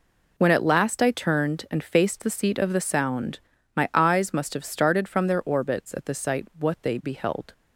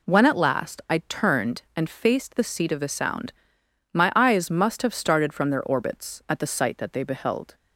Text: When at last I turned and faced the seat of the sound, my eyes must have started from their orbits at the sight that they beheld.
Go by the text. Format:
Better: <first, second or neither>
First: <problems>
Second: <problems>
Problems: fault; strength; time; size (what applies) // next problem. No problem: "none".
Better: second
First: says "what" for "that"; at 6.5 s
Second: none